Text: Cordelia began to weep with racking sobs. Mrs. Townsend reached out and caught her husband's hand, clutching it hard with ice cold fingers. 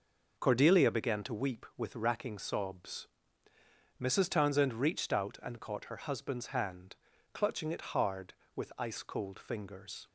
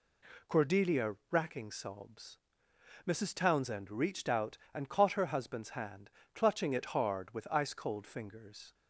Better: first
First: none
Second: skips "began to weep with"; at 1.2 s

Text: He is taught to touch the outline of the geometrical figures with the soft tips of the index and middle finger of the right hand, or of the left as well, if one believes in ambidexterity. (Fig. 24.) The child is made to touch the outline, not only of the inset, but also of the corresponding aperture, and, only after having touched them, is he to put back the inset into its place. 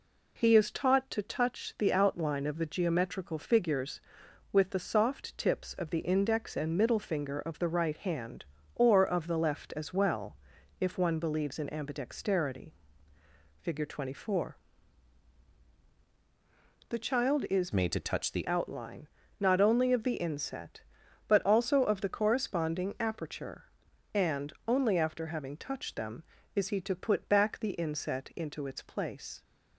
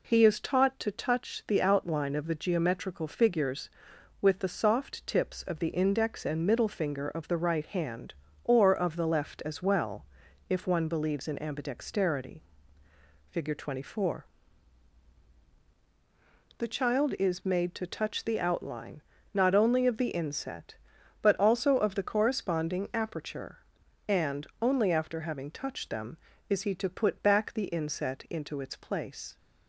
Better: second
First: changes voice from "made" to "the"; from 17.7 to 18.4 s; 0.7 s long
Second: none

